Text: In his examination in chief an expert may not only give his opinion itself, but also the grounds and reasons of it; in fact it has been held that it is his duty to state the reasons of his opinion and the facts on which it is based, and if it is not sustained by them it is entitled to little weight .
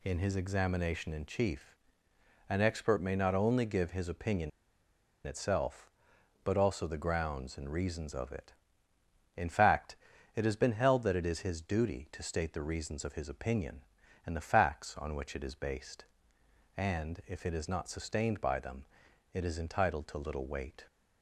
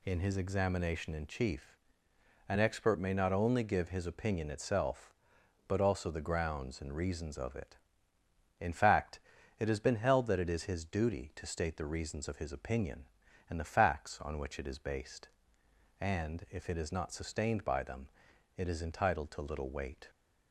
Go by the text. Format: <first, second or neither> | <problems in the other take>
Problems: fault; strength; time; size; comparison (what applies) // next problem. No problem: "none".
second | pauses between "chief" and "an"; noticeable; at 1.7 s; 0.74 s long; noticeable in the second // pauses between "opinion" and "itself"; noticeable; at 4.5 s; 0.76 s long // pauses between "fact" and "it"; at 9.9 s; 0.38 s long; also in the second // pauses between "them" and "it"; noticeable; at 18.8 s; 0.48 s long; noticeable in the second